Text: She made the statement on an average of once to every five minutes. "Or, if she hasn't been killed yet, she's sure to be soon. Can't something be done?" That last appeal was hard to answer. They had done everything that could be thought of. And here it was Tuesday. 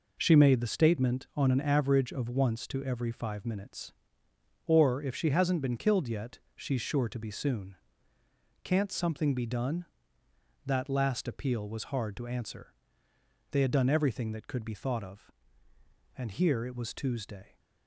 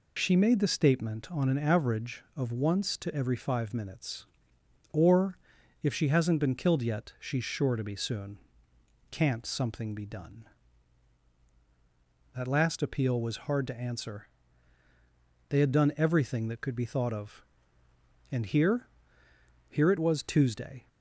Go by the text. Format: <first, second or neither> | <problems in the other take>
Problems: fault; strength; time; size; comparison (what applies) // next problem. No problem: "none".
first | says "here" twice; at 19.6 s